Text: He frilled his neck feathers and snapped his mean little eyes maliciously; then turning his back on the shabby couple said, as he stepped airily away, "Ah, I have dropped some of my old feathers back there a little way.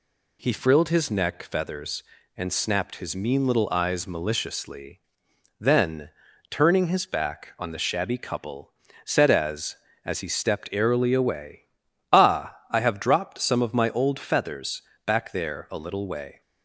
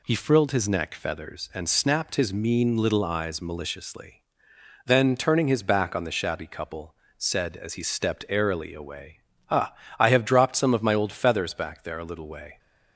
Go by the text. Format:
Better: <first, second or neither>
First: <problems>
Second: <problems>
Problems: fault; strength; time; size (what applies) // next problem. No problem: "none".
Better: second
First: pauses between "then" and "turning"; at 6.0 s; 0.40 s long // pauses between "couple" and "said"; slight; at 8.7 s; 0.34 s long // says "as" twice; at 10.0 s // pauses between "feathers" and "back"; slight; at 14.8 s; 0.24 s long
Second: pauses between "couple" and "said"; slight; at 6.9 s; 0.22 s long